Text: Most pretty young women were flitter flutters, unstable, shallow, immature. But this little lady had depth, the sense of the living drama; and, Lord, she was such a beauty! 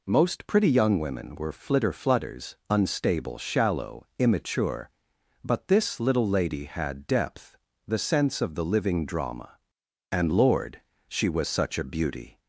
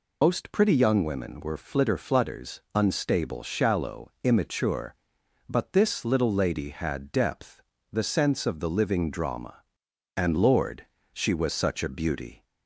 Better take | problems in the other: first | loses the start of "Most"; at 0.2 s; 120 ms

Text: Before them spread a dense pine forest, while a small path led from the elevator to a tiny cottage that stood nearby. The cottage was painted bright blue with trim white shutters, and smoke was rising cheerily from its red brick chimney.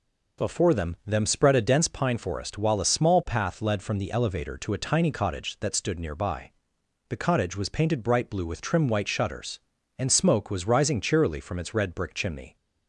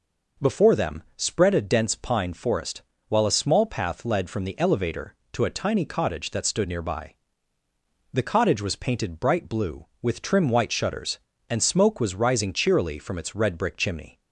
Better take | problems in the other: second | says "them" twice; at 1.0 s

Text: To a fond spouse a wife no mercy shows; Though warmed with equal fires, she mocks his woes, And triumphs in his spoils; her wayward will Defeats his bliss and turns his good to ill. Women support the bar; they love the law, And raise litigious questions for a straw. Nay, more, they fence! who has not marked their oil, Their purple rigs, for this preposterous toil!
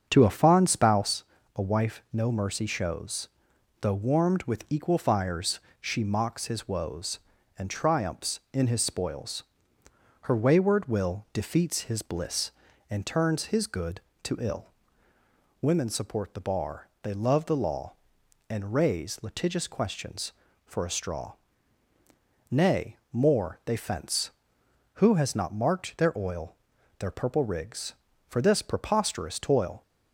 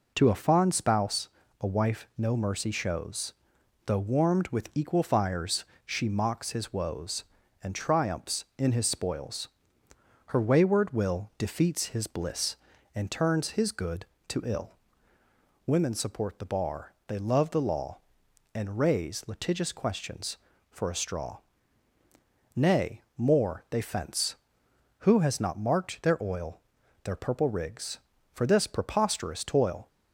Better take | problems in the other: second | starts louder than the rest; strong; until 1.2 s; 7 dB // pauses between "spouse" and "a"; slight; at 1.2 s; 0.32 s long; slight in the second

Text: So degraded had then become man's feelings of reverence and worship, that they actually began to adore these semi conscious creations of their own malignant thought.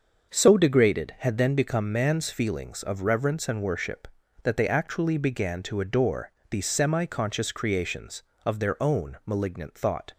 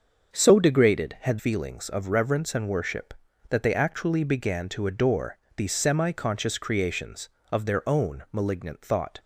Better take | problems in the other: first | starts louder than the rest; until 1.3 s; 6.5 dB; also in the first // skips "then become man's"; at 1.3 s // pauses between "adore" and "these"; slight; at 5.3 s; 0.20 s long; slight in the first

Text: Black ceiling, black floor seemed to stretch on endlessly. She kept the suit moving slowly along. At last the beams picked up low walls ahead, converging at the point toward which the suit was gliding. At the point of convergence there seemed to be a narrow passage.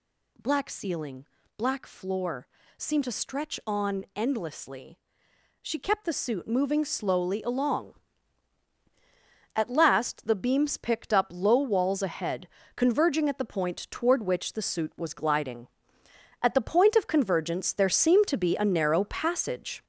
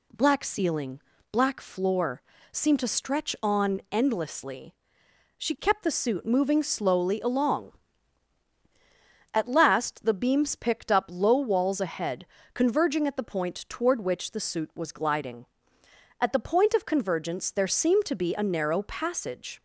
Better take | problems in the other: second | gets louder; noticeable; throughout; 5.5 dB // pauses between "floor" and "seemed"; slight; at 2.4 s; 0.30 s long; slight in the second

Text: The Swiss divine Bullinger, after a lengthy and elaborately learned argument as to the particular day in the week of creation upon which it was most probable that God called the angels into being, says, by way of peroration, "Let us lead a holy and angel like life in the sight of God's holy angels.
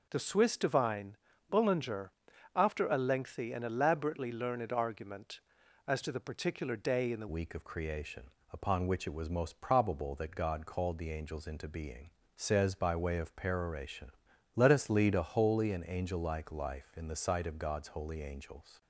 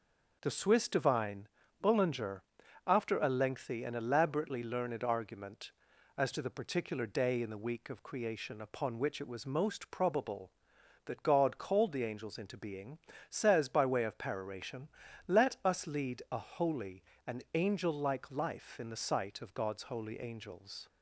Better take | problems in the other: second | pauses between "divine" and "Bullinger"; slight; at 1.1 s; 0.34 s long; slight in the second // changes voice at "week"; from 7.2 s on; 11.6 s long // pauses between "creation" and "upon"; slight; at 8.3 s; 0.20 s long

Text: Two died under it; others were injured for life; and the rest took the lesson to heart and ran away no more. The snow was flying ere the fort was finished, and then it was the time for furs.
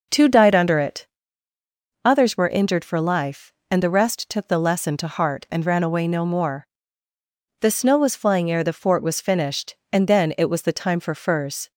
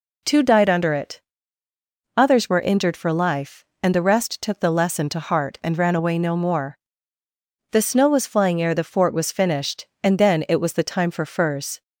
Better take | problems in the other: second | starts louder than the rest; noticeable; until 1.7 s; 5.5 dB

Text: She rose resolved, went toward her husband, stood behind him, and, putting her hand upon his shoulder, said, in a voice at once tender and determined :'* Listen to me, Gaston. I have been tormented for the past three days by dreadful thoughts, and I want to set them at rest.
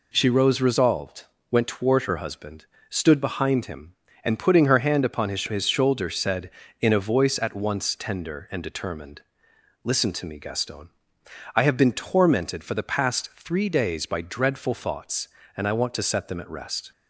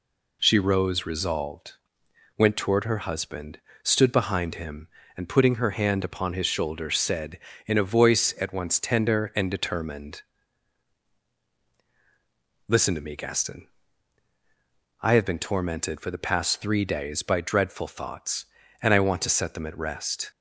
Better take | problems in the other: second | says "his" twice; at 5.4 s

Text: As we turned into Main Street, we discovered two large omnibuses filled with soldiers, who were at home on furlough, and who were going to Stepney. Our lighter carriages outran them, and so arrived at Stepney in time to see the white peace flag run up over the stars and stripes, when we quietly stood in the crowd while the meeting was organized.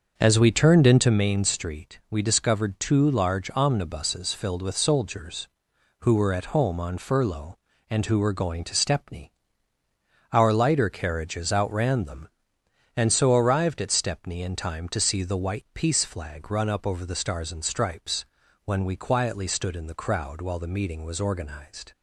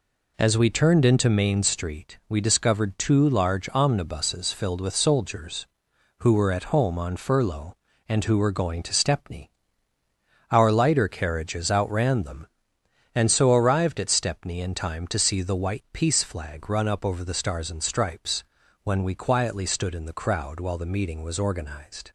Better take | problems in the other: second | starts louder than the rest; until 1.2 s; 6.5 dB

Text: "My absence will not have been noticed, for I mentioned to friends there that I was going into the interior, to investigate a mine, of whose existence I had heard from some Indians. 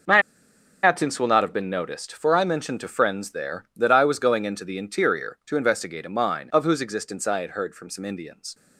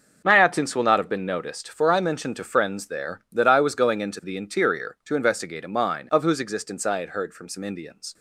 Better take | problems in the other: second | pauses between "My" and "absence"; noticeable; at 0.2 s; 0.61 s long

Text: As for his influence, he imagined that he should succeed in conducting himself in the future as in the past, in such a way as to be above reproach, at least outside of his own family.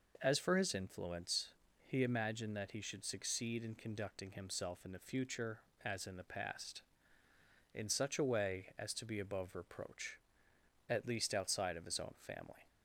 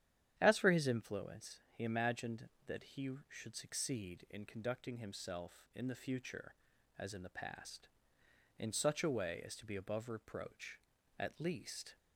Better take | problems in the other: first | starts louder than the rest; strong; until 1.3 s; 10.5 dB // stops before "outside of his own family"; at 11.9 s

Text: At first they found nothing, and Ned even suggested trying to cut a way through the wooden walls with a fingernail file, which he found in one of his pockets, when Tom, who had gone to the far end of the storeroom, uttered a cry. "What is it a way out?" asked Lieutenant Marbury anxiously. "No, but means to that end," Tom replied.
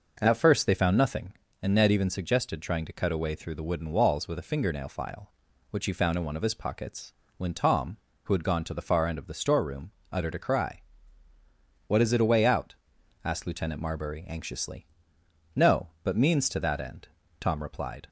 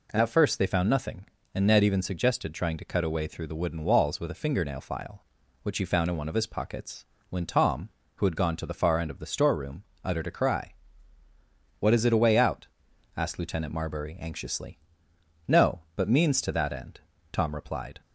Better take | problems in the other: second | starts louder than the rest; noticeable; until 1.3 s; 5.5 dB

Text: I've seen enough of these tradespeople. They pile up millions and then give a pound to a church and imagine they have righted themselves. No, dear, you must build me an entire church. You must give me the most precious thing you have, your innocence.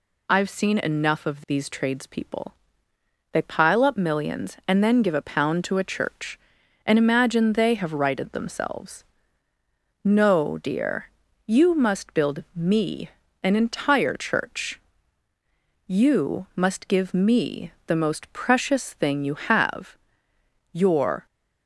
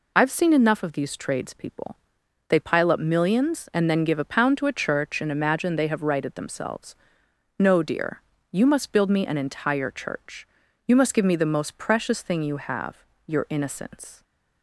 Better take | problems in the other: second | pauses between "me" and "an"; slight; at 13.0 s; 0.32 s long // pauses between "me" and "the"; slight; at 17.7 s; 0.16 s long // stops before "innocence"; at 21.2 s

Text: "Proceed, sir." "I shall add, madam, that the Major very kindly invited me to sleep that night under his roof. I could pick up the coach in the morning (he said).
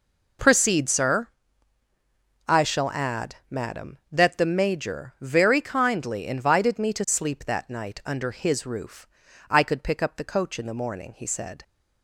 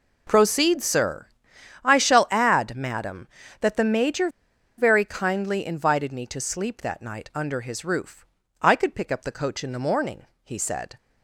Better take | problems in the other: first | pauses between "Major" and "very"; noticeable; at 4.2 s; 0.49 s long

